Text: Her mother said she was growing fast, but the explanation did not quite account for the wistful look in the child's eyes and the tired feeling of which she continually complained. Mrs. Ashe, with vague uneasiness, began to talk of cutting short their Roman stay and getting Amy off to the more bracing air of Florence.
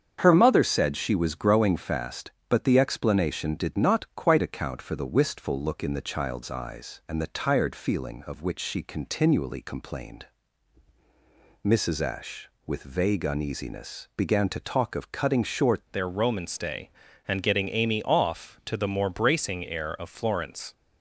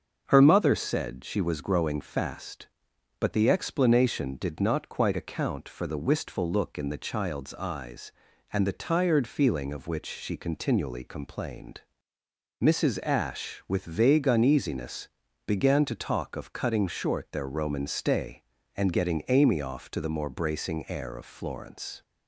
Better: second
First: starts louder than the rest; strong; until 1.2 s; 7.5 dB // changes voice at "their"; from 15.9 s on; 4.8 s long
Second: starts louder than the rest; until 1.2 s; 6.5 dB

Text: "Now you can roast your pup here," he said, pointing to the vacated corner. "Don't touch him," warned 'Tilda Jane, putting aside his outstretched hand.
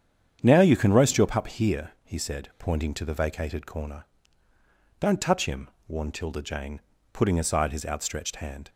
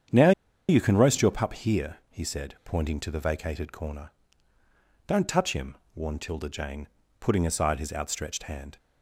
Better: first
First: starts louder than the rest; strong; until 1.4 s; 8.5 dB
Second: starts louder than the rest; strong; until 1.4 s; 8.5 dB // pauses between "Now" and "you"; at 0.3 s; 0.37 s long

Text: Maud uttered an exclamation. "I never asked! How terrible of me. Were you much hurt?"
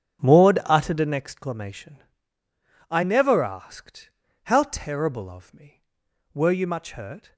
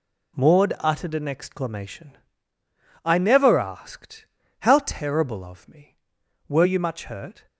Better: second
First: starts louder than the rest; strong; until 1.4 s; 8 dB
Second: none

